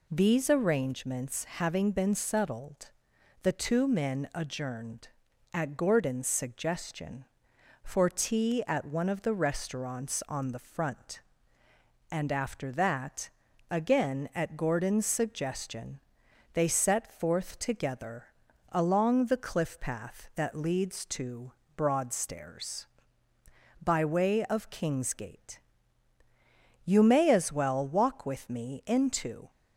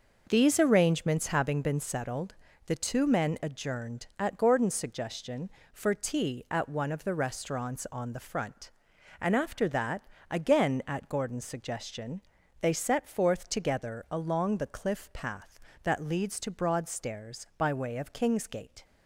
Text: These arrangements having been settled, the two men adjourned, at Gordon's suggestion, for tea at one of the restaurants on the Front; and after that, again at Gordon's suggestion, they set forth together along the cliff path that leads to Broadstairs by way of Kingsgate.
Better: second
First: pauses between "together" and "along"; at 18.2 s; 0.44 s long // pauses between "to" and "Broadstairs"; slight; at 21.5 s; 0.24 s long // goes on to say "You may as well walk with me into"; strong; from 26.8 s on; 2.6 s long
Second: none

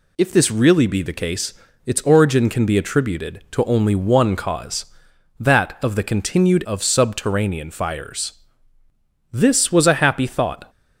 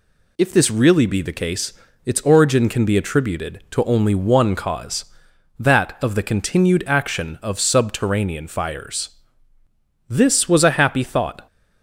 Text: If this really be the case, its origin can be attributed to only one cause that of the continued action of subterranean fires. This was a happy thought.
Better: second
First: skips "action"; at 6.6 s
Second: none

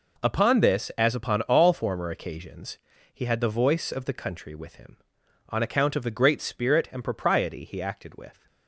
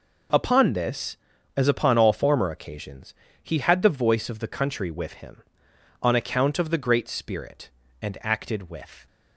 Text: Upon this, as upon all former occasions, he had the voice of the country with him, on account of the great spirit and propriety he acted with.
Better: first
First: none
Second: skips "propriety he"; at 8.1 s

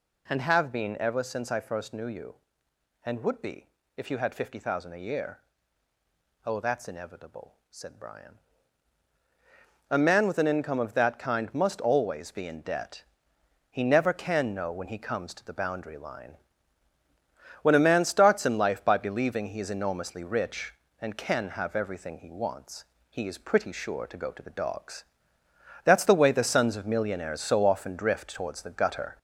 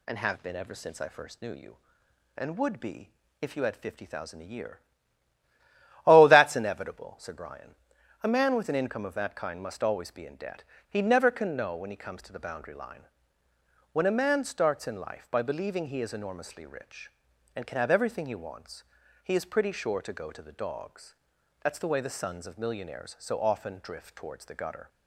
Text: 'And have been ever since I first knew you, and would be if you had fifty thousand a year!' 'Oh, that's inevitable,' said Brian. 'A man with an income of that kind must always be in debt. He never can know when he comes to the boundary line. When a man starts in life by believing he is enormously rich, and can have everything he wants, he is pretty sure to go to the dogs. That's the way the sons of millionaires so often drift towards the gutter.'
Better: second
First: gets louder; slight; throughout; 3 dB // pauses between "be" and "if"; slight; at 3.6 s; 0.28 s long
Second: pauses between "be" and "if"; slight; at 3.1 s; 0.30 s long

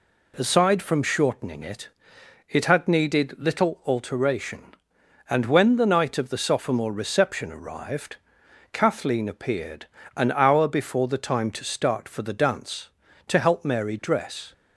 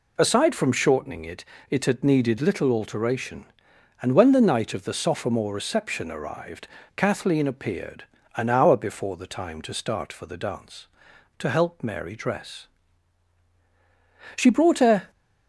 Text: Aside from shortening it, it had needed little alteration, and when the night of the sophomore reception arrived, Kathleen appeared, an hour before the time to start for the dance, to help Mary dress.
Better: first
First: none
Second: goes on to say "She brought a"; noticeable; from 14.3 s on; 0.74 s long

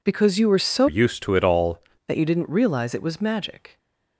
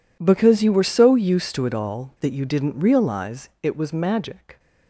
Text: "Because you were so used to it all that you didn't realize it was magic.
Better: second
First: changes voice from "used" to "all"; from 0.8 to 1.8 s; 1.0 s long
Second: none

